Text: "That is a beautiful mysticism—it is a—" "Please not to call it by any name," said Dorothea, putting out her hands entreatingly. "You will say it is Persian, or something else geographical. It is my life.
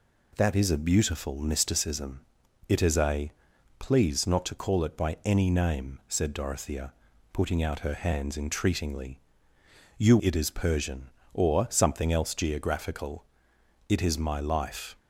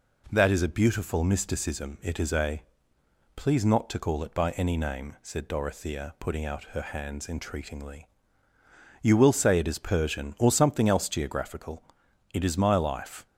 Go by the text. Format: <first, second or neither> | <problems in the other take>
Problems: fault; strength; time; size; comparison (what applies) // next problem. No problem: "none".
second | skips "will say"; at 10.1 s